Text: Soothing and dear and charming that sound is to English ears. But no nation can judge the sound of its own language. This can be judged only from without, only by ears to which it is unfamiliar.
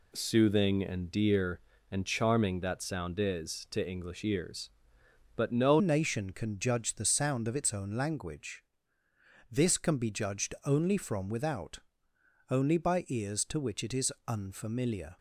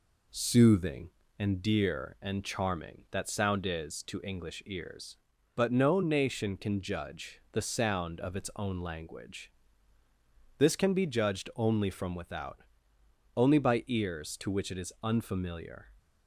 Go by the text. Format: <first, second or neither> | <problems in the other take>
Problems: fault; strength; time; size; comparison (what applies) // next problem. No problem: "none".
second | changes voice at "nation"; from 5.7 s on; 9.4 s long // pauses between "is" and "unfamiliar"; slight; at 14.1 s; 0.16 s long